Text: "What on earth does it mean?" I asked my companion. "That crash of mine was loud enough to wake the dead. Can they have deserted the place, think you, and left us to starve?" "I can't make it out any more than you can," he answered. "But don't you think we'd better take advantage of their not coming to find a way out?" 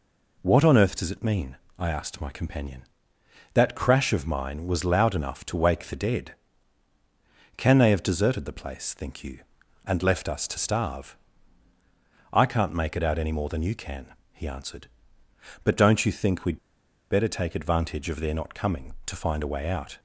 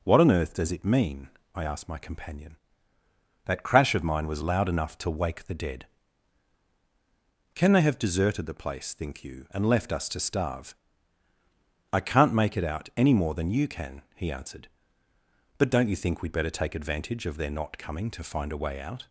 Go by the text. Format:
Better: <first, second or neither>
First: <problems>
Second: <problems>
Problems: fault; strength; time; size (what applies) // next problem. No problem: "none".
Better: second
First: pauses between "we'd" and "better"; noticeable; at 16.5 s; 0.53 s long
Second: none